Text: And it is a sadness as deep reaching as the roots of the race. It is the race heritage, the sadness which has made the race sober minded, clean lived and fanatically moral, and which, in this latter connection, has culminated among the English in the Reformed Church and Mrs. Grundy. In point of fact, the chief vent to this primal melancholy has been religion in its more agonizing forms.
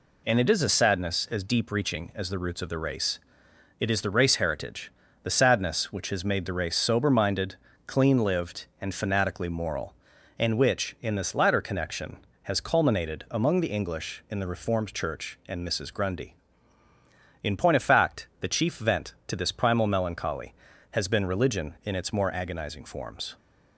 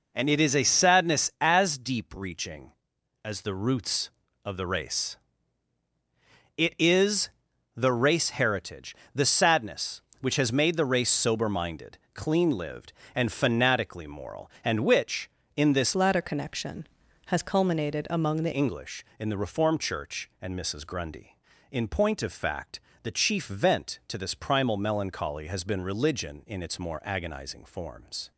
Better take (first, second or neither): first